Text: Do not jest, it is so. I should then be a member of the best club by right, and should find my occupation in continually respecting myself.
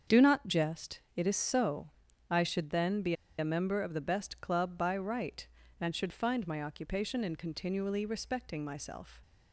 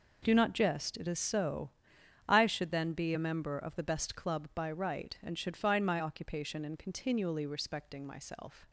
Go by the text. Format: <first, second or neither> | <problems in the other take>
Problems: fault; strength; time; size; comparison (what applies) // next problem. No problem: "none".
second | starts louder than the rest; strong; until 1.2 s; 7 dB // pauses between "be" and "a"; slight; at 3.1 s; 0.26 s long